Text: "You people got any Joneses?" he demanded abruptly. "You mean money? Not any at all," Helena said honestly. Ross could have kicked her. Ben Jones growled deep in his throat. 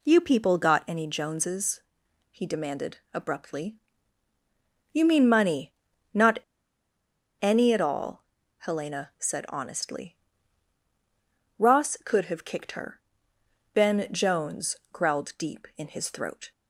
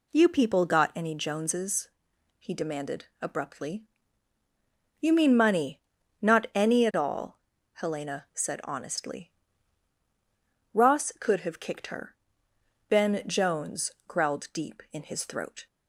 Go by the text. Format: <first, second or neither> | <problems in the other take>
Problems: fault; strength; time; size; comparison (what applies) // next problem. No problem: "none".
second | pauses between "demanded" and "abruptly"; slight; at 2.9 s; 0.16 s long; slight in the second // pauses between "Not" and "any"; at 6.3 s; 1.0 s long // pauses between "Jones" and "growled"; slight; at 14.7 s; 0.16 s long; slight in the second